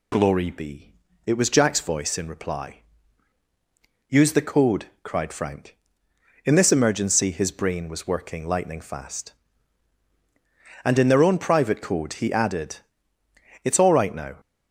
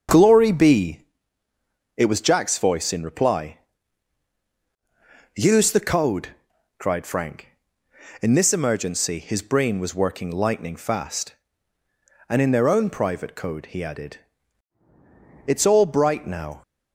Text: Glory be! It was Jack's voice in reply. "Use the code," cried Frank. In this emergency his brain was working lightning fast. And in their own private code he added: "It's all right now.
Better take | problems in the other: first | starts louder than the rest; until 2.0 s; 7 dB // says "bright" for "right"; at 15.8 s

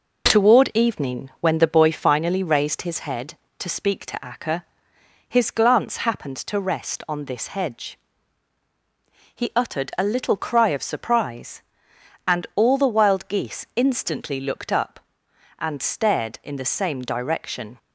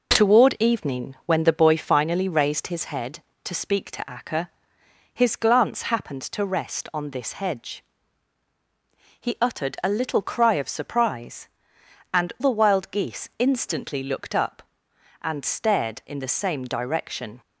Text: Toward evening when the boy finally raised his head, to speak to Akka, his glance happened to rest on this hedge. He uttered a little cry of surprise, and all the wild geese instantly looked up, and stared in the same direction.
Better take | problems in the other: first | skips "all"; at 12.3 s

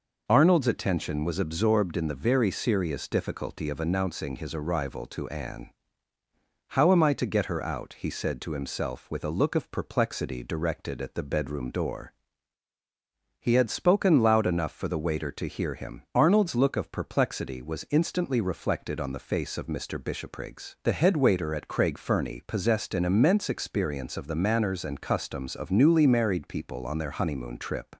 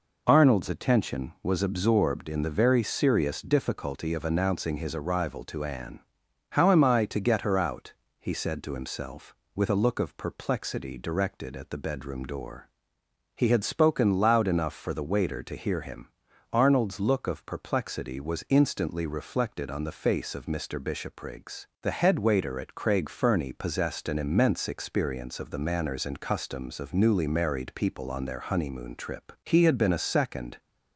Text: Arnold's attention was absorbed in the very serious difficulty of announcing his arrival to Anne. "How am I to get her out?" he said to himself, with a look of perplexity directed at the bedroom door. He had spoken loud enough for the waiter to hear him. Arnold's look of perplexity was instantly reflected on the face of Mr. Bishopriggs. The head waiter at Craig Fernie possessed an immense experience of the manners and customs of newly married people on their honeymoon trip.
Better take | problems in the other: first | goes on to say "He had been a second"; noticeable; from 29.4 s on; 1.1 s long

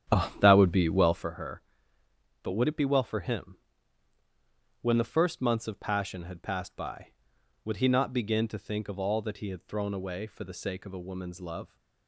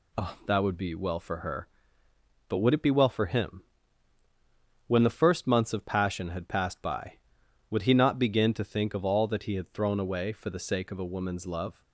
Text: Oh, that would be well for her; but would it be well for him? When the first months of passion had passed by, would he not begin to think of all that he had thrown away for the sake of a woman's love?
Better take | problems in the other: second | starts louder than the rest; strong; until 1.3 s; 9.5 dB

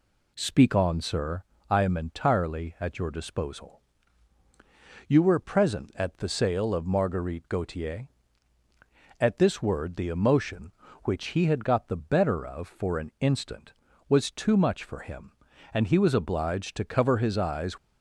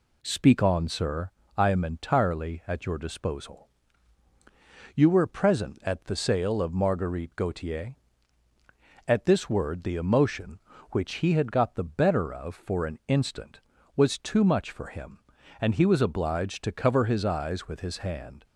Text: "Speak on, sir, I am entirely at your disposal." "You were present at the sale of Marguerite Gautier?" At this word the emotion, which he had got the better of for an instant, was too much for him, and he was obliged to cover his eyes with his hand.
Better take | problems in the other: second | stops before "with his hand"; at 17.7 s

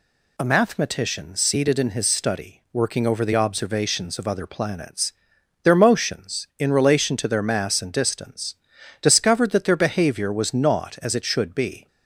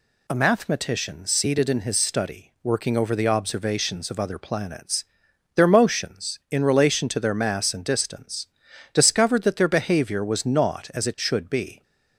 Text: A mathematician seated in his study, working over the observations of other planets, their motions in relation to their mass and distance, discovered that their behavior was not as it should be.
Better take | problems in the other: neither | none

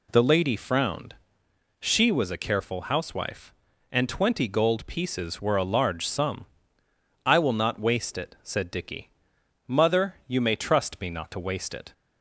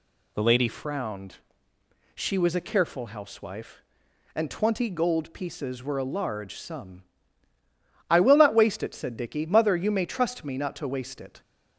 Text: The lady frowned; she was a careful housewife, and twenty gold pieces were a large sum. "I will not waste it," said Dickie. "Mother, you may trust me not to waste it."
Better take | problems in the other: first | changes voice at "frowned"; from 0.6 s on; 10.8 s long

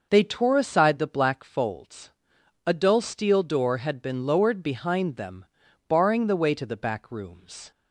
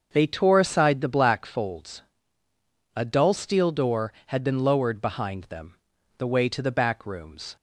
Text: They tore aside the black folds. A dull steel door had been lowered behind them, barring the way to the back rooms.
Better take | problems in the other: first | starts louder than the rest; until 1.1 s; 6.5 dB // skips "barring"; at 5.9 s

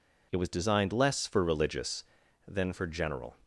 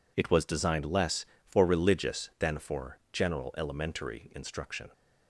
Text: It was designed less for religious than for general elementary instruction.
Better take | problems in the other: second | stops before "elementary instruction"; at 3.4 s

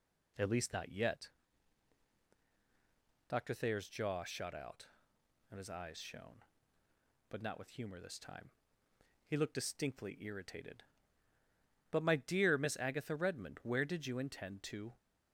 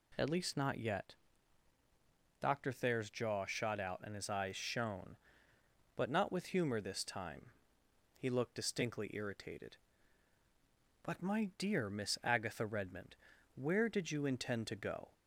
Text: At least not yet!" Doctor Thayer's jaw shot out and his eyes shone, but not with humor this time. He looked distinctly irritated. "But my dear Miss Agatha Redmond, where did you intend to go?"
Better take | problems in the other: second | stops before "go"; at 14.9 s

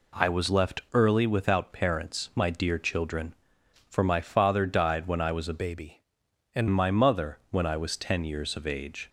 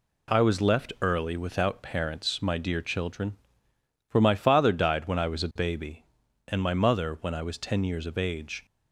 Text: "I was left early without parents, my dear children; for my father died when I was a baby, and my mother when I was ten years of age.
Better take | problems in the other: second | changes voice from "baby" to "and"; from 5.5 to 6.6 s; 1.1 s long

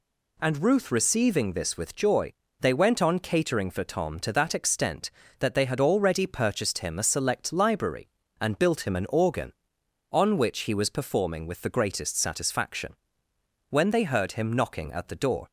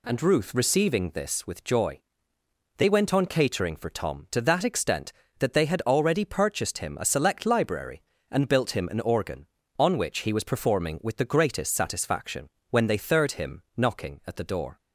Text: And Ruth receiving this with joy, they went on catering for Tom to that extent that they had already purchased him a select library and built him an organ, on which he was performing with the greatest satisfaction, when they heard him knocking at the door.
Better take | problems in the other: first | says "third" for "heard"; at 12.9 s

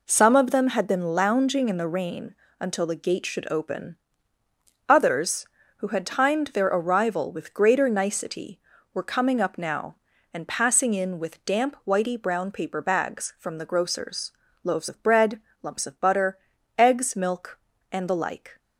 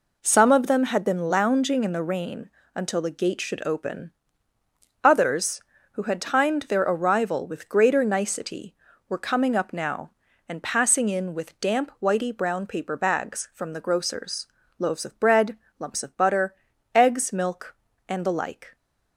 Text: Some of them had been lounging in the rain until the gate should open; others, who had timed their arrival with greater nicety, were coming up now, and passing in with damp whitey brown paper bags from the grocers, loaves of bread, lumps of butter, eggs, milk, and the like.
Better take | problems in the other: neither | pauses between "rain" and "until"; slight; the same in both

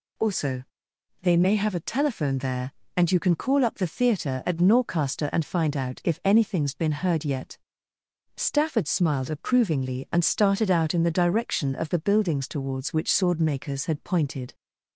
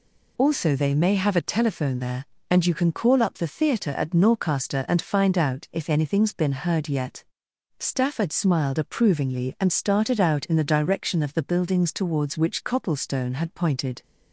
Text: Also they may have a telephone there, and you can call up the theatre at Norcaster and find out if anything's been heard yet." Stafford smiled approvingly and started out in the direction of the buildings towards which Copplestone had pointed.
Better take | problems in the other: second | pauses between "Also" and "they"; noticeable; at 0.6 s; 0.58 s long // says "Swordmakers" for "Copplestone"; at 13.1 s

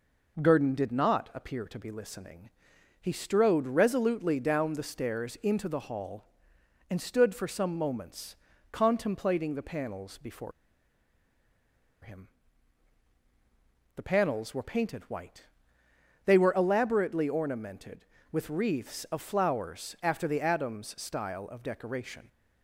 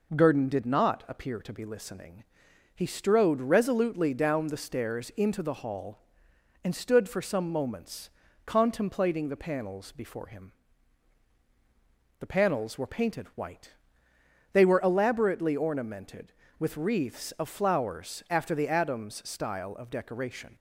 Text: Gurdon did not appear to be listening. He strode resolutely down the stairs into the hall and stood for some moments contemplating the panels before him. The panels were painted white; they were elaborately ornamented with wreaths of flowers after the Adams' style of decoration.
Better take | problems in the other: second | pauses between "moments" and "contemplating"; slight; at 8.3 s; 0.34 s long; slight in the second // pauses between "before" and "him"; strong; at 10.5 s; 1.5 s long

